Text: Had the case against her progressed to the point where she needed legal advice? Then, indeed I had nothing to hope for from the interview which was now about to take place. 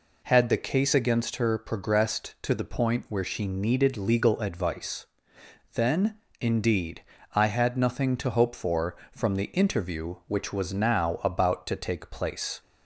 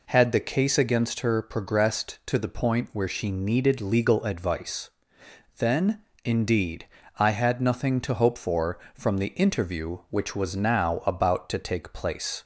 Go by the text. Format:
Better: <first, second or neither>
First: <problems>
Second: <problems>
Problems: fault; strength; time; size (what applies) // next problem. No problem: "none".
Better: neither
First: pauses between "indeed" and "I"; slight; at 7.0 s; 0.32 s long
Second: pauses between "indeed" and "I"; slight; at 6.8 s; 0.32 s long